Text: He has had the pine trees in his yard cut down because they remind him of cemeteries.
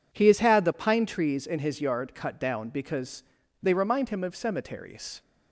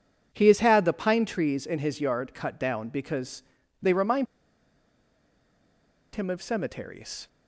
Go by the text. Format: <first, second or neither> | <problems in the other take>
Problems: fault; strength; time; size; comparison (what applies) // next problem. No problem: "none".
first | pauses between "because" and "they"; at 3.4 s; 0.38 s long; also in the first // pauses between "remind" and "him"; strong; at 4.2 s; 1.8 s long